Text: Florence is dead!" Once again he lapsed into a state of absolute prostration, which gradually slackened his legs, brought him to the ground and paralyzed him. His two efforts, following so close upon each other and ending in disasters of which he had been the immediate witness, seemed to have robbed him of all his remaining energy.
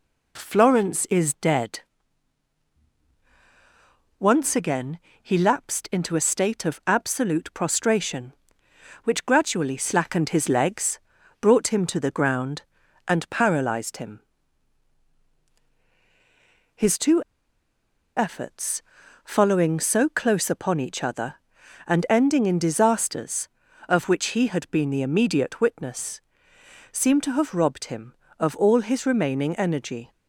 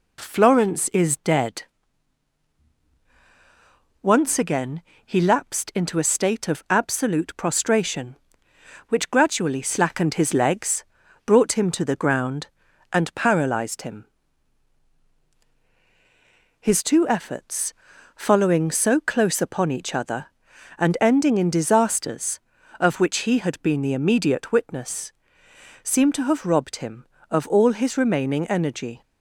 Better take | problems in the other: second | pauses between "again" and "he"; slight; at 4.9 s; 0.22 s long; slight in the second // pauses between "two" and "efforts"; noticeable; at 17.2 s; 0.94 s long

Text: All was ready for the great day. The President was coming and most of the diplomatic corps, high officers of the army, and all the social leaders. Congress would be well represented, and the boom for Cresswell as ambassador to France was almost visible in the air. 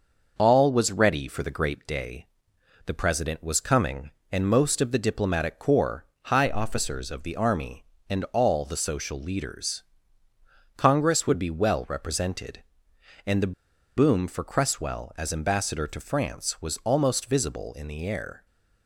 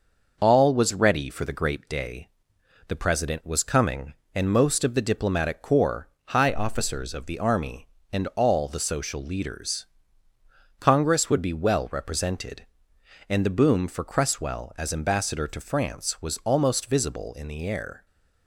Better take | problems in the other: second | pauses between "the" and "boom"; at 13.5 s; 0.44 s long

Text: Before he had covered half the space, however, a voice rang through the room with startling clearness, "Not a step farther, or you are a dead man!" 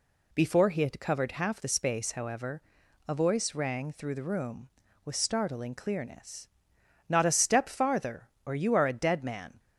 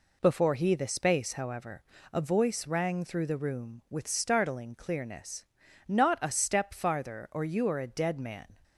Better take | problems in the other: first | skips "had covered half"; at 0.7 s

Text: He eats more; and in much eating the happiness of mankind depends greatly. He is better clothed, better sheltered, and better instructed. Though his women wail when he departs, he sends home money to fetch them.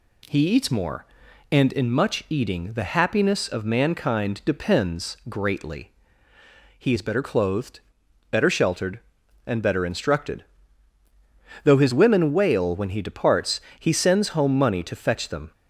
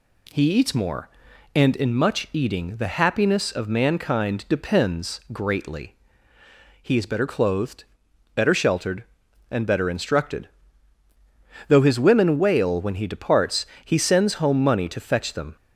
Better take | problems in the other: neither | none

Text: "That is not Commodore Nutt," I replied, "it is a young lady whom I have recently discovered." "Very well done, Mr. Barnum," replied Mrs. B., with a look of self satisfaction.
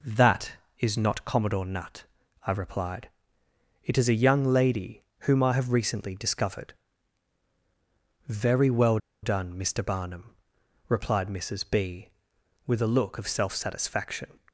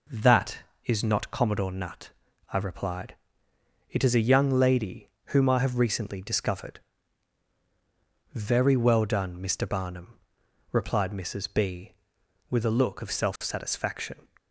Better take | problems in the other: second | pauses between "lady" and "whom"; slight; at 5.0 s; 0.22 s long; slight in the second // pauses between "well" and "done"; slight; at 8.9 s; 0.25 s long

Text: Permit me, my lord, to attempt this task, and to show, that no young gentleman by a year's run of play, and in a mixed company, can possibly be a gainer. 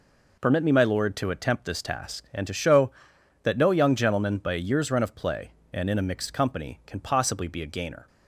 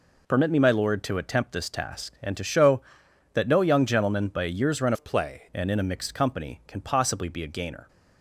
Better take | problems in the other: first | changes voice from "of" to "play"; from 4.9 to 5.4 s; 0.5 s long

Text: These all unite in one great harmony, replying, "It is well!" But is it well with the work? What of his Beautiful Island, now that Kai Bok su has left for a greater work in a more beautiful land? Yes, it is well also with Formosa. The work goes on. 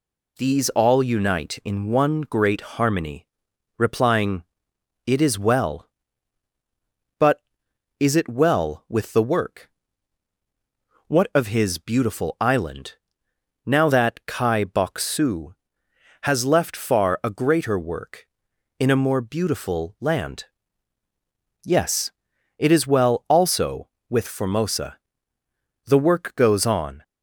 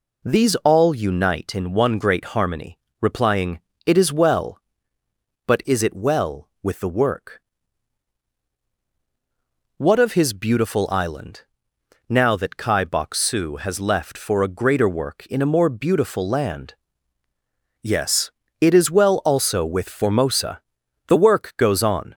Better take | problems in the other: second | says "far" for "for"; at 16.7 s

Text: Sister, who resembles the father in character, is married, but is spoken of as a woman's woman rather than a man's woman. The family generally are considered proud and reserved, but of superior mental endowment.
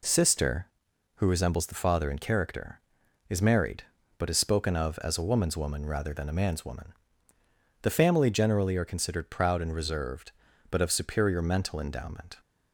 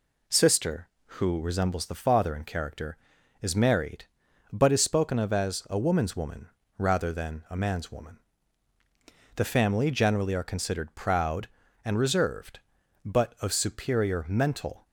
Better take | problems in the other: first | pauses between "woman" and "rather"; slight; at 6.4 s; 0.28 s long // stops before "endowment"; at 14.8 s

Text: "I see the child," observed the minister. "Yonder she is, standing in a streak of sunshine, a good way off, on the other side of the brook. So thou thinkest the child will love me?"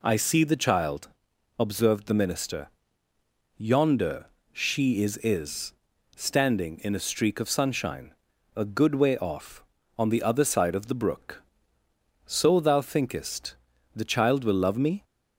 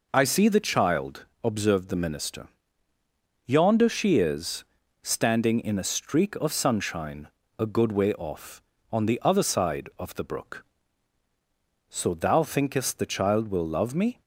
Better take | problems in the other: second | pauses between "Yonder" and "she"; slight; at 4.2 s; 0.26 s long // says "is" twice; at 5.1 s // pauses between "thinkest" and "the"; at 13.5 s; 0.40 s long

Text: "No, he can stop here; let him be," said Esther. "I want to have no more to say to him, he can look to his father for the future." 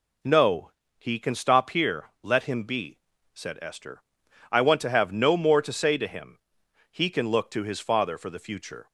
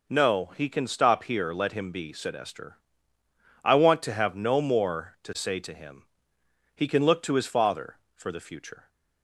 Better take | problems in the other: neither | none

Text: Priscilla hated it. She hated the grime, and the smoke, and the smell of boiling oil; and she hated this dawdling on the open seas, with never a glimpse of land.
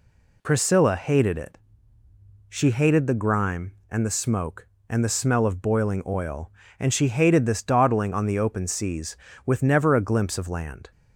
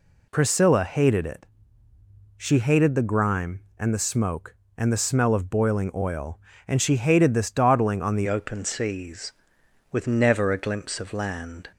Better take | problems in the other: first | changes voice at "open"; from 8.2 s on; 3.4 s long

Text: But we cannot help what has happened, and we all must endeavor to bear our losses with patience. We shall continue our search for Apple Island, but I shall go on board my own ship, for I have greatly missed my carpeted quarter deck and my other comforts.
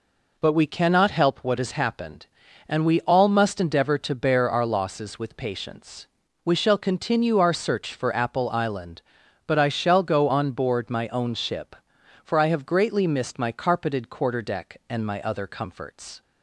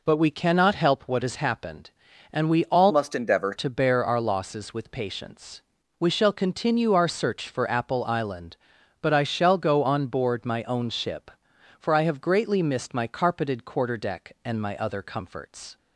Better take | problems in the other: first | changes voice from "must" to "endeavor"; from 2.8 to 3.5 s; 0.7 s long

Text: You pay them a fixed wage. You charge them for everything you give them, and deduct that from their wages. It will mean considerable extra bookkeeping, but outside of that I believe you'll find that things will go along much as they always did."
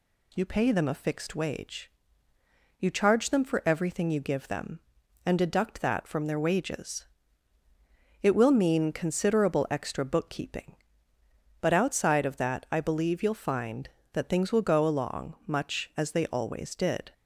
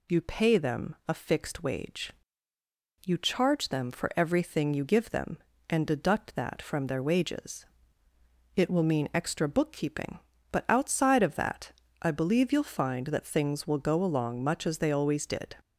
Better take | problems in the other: first | skips "considerable"; at 9.1 s // pauses between "that" and "I"; slight; at 11.7 s; 0.30 s long

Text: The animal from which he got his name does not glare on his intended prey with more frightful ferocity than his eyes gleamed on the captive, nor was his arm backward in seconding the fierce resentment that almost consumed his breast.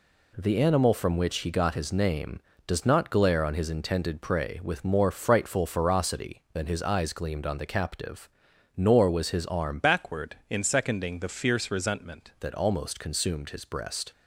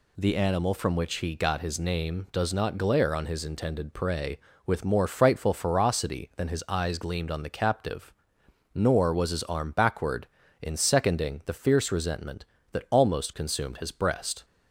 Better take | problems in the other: second | changes voice from "backward" to "resentment"; from 9.7 to 12.3 s; 2.6 s long

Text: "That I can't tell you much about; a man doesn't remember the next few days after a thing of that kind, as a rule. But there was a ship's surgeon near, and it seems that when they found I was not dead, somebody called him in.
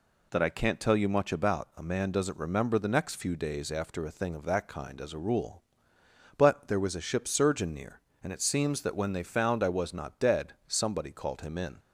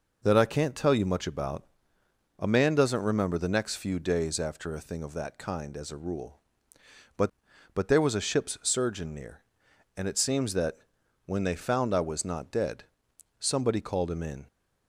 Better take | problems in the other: first | says "But" twice; at 7.7 s // pauses between "that" and "when"; noticeable; at 10.7 s; 0.48 s long

